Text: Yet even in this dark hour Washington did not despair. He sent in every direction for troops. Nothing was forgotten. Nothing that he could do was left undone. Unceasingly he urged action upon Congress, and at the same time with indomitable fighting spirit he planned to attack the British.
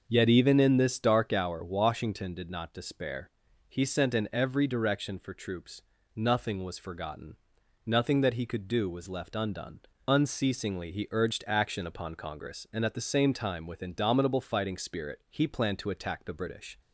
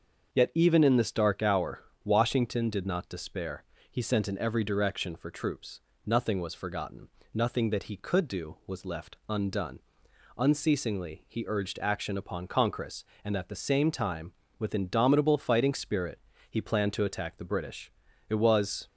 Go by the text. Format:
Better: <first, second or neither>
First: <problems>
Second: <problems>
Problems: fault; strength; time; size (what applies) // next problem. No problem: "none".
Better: first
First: starts louder than the rest; until 1.1 s; 6 dB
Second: starts louder than the rest; until 1.3 s; 6.5 dB // pauses between "hour" and "Washington"; slight; at 1.8 s; 0.22 s long // pauses between "spirit" and "he"; slight; at 16.1 s; 0.32 s long // goes on to say "It was"; from 18.2 s on; 0.58 s long